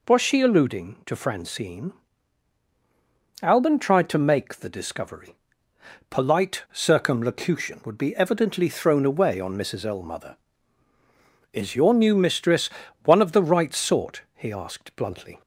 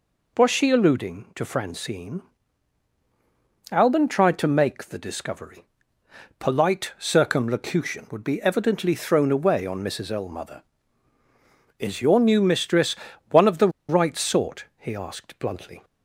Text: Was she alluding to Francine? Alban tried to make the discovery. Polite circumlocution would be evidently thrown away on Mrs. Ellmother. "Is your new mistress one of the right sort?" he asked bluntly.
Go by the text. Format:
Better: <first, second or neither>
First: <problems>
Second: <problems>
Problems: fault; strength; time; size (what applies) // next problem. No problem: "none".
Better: first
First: pauses between "mistress" and "one"; slight; at 12.6 s; 0.34 s long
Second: pauses between "mistress" and "one"; slight; at 12.9 s; 0.34 s long // pauses between "the" and "right"; slight; at 13.6 s; 0.19 s long